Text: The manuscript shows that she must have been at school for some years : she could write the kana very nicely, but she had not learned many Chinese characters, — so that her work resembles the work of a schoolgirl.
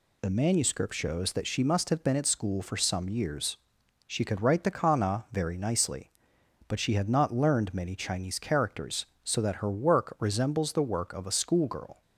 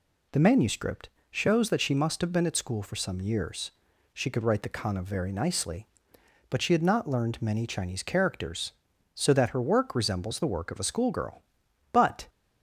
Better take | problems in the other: first | pauses between "manuscript" and "shows"; slight; at 1.0 s; 0.22 s long // goes on to say "But"; slight; from 11.9 s on; 0.34 s long

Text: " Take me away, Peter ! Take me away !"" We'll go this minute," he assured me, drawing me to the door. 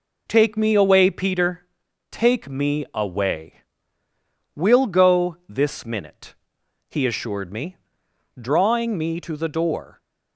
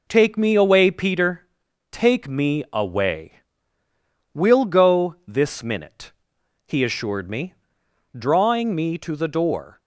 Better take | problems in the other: neither | none

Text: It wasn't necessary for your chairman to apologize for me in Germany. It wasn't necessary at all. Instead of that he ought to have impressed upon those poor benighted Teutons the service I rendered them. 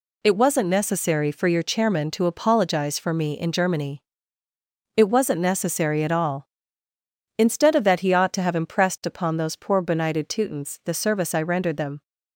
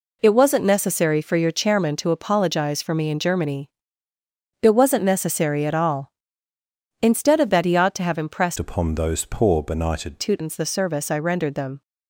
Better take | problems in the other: first | changes voice from "upon" to "benighted"; from 8.5 to 10.1 s; 1.6 s long

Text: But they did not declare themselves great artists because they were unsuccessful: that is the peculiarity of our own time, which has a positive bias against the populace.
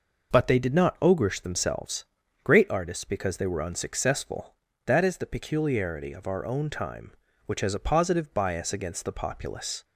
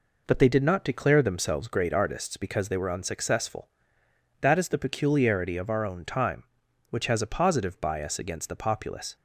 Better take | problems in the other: second | says "ogreish" for "declare"; at 0.9 s // pauses between "themselves" and "great"; slight; at 2.0 s; 0.36 s long

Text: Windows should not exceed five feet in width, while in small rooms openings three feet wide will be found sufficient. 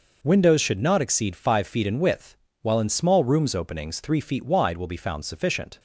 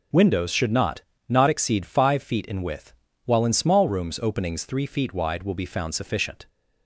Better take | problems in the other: first | starts louder than the rest; strong; until 1.4 s; 7.5 dB // says "not" twice; at 1.2 s

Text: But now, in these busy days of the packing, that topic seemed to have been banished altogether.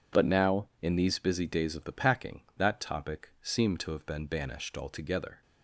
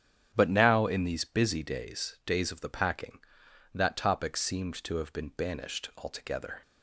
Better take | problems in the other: first | starts louder than the rest; strong; until 1.3 s; 9 dB // says "days" twice; at 2.2 s

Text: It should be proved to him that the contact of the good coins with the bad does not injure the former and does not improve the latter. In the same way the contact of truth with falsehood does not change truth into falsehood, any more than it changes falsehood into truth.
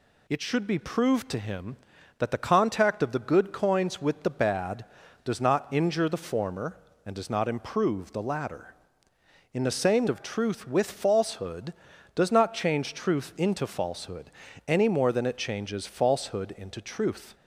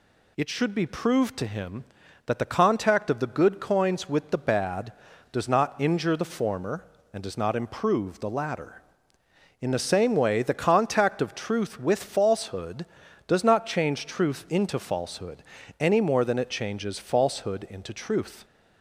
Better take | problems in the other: second | skips "way the contact"; at 10.0 s

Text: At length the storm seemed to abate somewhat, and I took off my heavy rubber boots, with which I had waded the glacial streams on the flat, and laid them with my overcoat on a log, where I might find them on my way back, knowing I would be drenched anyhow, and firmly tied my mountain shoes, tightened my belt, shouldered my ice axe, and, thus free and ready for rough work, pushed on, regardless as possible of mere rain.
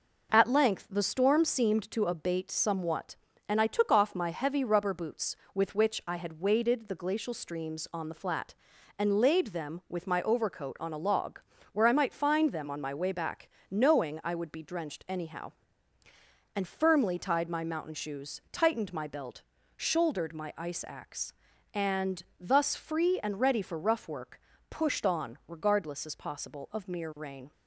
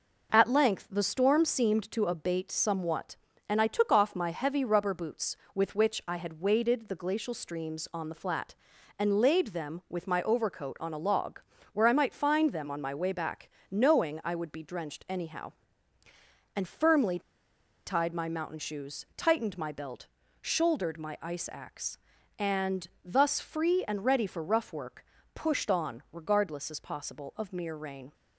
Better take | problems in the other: first | pauses between "firmly" and "tied"; noticeable; at 17.1 s; 0.67 s long

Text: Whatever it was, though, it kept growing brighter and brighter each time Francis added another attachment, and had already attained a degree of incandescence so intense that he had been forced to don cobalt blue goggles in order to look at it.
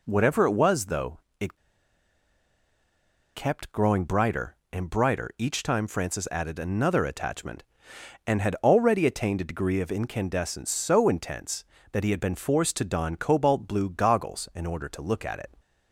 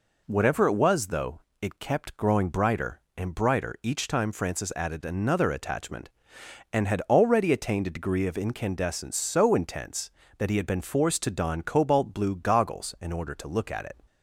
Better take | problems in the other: second | pauses between "it" and "kept"; strong; at 1.5 s; 1.7 s long

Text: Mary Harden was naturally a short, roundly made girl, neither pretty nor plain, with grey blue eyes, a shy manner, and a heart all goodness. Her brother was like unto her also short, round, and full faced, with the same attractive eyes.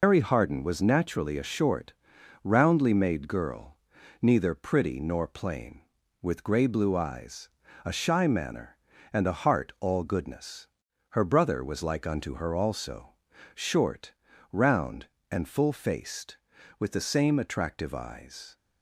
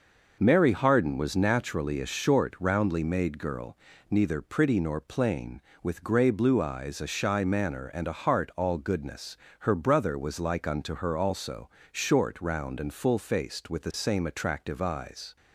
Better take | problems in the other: second | loses the start of "Mary"; at 0.0 s; 140 ms // pauses between "also" and "short"; at 13.1 s; 0.40 s long; slight in the second

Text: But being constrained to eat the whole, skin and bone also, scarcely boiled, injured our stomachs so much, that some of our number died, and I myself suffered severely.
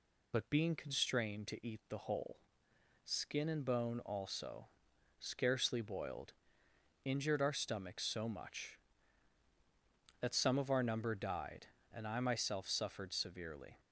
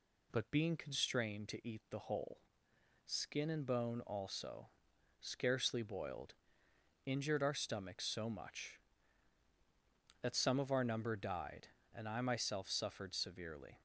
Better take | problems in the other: second | loses the start of "But"; at 0.3 s; 50 ms

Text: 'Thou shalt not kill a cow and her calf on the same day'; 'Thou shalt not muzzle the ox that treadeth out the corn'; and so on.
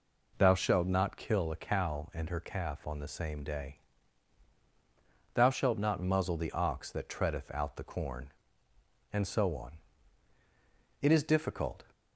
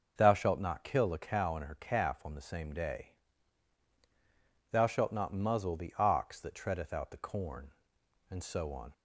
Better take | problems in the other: second | goes on to say "It is difficult"; noticeable; from 11.0 s on; 0.84 s long

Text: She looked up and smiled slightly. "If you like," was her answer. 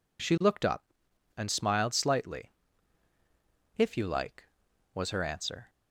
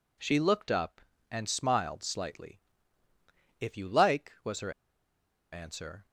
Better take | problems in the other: first | pauses between "her" and "answer"; noticeable; at 4.7 s; 0.80 s long

